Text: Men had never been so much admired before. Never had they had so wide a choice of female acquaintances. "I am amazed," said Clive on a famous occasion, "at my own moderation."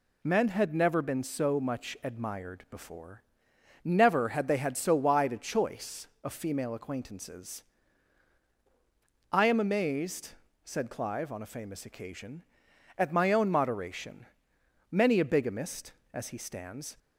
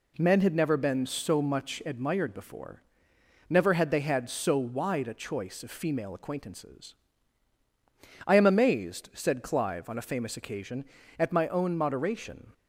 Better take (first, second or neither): second